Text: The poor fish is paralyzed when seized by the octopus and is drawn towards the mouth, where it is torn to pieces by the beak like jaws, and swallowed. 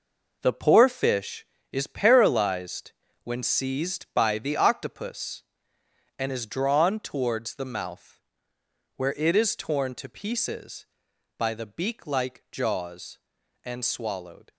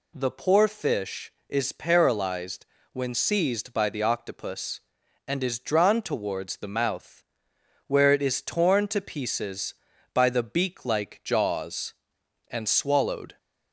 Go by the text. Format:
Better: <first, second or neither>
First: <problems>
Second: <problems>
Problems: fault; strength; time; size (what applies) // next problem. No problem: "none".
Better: second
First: gets quieter; strong; throughout; 9 dB // pauses between "paralyzed" and "when"; slight; at 2.9 s; 0.32 s long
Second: pauses between "paralyzed" and "when"; slight; at 2.6 s; 0.26 s long